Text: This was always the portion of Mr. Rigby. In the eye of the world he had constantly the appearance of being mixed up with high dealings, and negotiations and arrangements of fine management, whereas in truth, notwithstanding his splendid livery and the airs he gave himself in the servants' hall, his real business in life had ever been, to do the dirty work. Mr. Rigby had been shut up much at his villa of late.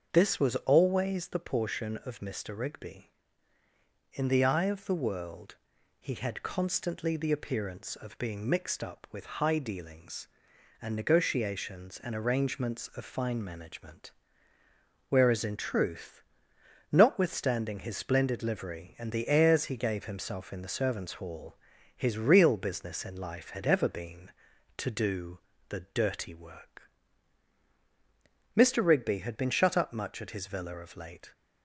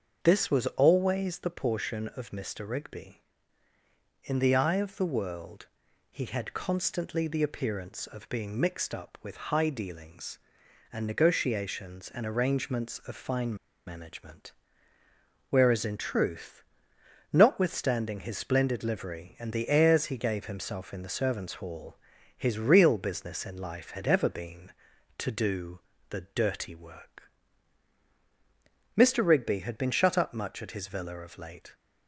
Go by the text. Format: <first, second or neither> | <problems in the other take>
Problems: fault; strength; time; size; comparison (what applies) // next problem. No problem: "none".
first | starts louder than the rest; until 1.2 s; 6.5 dB; also in the first // pauses between "world" and "he"; noticeable; at 5.6 s; 0.46 s long; noticeable in the first // pauses between "fine" and "management"; slight; at 13.5 s; 0.31 s long // pauses between "do" and "the"; slight; at 25.7 s; 0.30 s long; slight in the first